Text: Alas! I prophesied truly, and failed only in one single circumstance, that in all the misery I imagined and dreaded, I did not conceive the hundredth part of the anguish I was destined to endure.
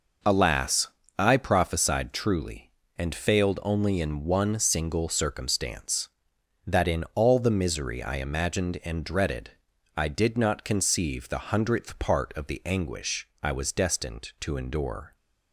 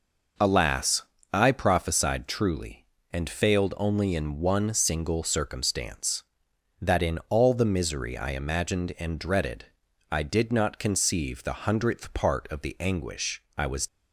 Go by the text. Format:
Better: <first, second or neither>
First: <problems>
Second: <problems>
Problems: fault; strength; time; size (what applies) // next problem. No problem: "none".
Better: first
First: none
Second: stops before "destined to endure"; at 13.8 s